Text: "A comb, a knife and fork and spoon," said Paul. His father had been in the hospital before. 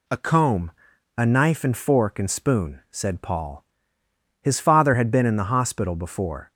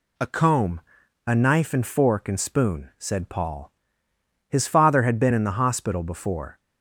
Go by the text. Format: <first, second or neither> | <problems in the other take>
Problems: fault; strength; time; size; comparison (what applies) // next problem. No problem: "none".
neither | none